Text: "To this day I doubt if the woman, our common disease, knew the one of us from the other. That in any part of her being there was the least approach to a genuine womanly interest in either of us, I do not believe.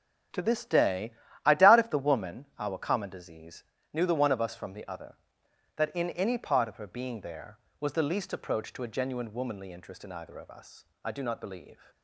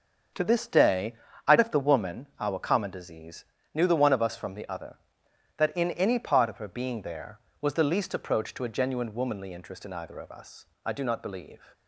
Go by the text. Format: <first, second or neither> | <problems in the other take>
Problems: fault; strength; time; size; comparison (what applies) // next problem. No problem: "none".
first | starts louder than the rest; until 1.6 s; 6.5 dB; also in the first // pauses between "day" and "I"; slight; at 1.1 s; 0.32 s long; slight in the first // skips "doubt"; at 1.5 s